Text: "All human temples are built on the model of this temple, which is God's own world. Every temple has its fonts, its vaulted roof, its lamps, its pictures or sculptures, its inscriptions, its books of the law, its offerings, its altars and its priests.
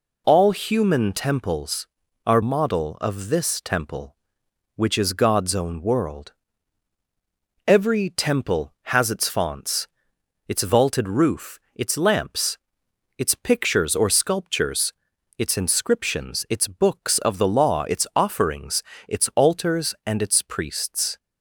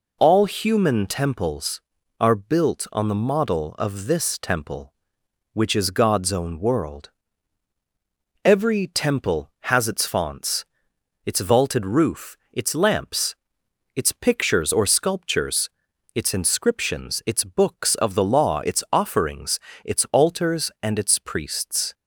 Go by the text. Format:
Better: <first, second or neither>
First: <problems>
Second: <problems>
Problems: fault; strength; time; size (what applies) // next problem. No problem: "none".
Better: second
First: skips "built on the"; at 2.4 s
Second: none